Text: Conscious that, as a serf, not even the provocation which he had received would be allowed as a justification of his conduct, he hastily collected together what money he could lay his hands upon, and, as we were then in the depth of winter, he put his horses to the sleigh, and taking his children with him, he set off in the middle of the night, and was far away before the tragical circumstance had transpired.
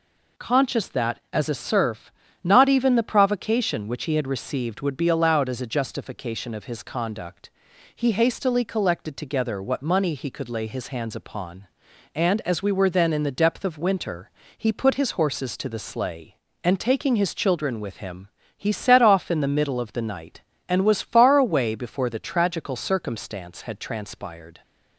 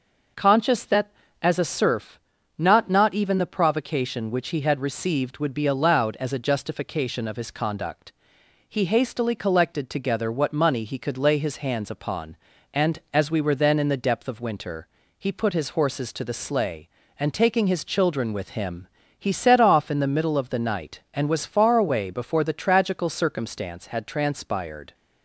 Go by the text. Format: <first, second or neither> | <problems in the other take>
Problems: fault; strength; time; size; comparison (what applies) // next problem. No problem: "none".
first | says "not" twice; at 2.8 s